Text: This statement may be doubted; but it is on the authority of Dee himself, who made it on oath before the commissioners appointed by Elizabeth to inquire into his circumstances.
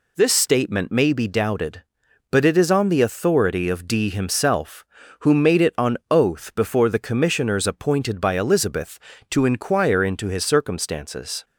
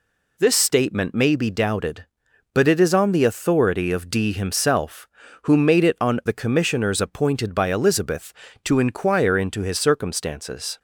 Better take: first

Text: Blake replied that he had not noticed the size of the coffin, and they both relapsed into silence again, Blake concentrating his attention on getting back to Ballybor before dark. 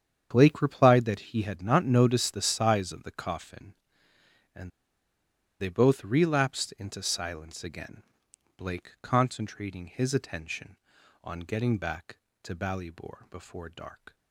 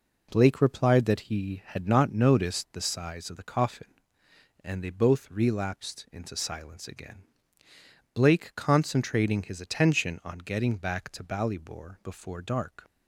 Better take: second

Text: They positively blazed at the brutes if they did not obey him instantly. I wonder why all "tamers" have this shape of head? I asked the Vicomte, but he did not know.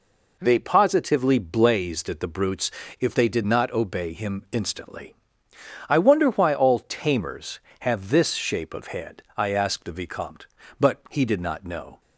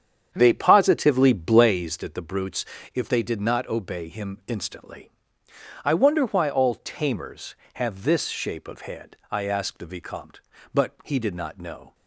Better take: first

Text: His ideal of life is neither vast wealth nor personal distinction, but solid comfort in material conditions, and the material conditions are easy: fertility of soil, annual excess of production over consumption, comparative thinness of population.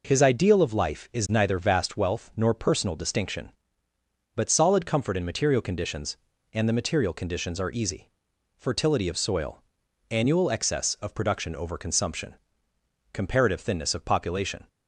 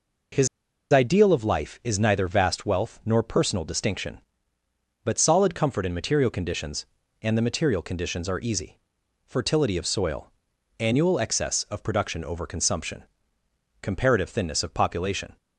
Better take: first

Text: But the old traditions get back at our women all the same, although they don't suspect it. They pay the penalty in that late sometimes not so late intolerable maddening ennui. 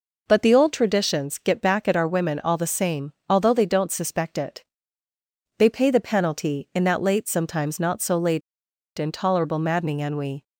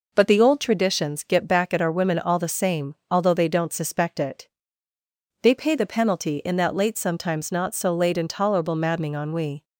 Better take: second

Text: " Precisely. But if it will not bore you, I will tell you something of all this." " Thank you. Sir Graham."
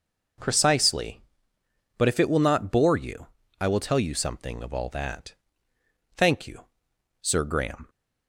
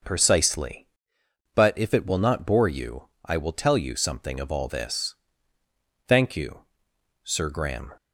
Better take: second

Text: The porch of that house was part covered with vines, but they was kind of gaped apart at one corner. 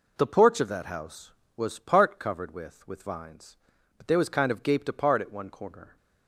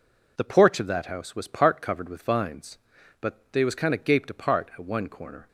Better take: second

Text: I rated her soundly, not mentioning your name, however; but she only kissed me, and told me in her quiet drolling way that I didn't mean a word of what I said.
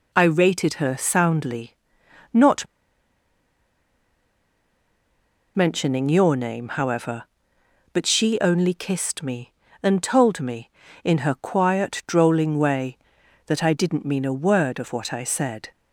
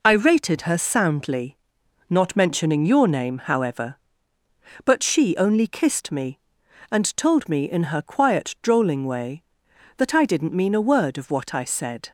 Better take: second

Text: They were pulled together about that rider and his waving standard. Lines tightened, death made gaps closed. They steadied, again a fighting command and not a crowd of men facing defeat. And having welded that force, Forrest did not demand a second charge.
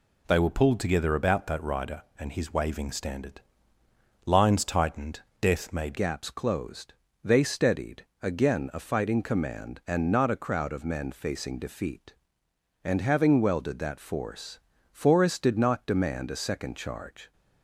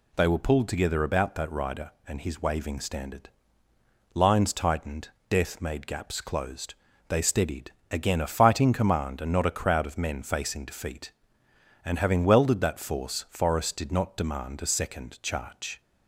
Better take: second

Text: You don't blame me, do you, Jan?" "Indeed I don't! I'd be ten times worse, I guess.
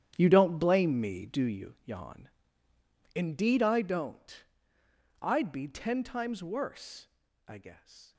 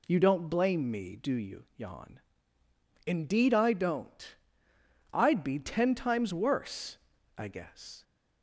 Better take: second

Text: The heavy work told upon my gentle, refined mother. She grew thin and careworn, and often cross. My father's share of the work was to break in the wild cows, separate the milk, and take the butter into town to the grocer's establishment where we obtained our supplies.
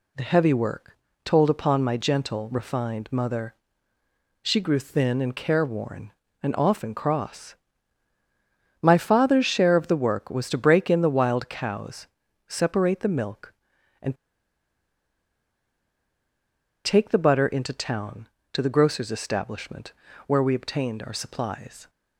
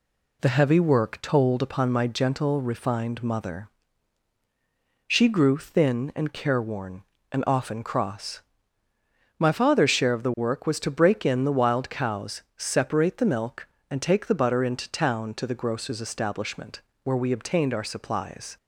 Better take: second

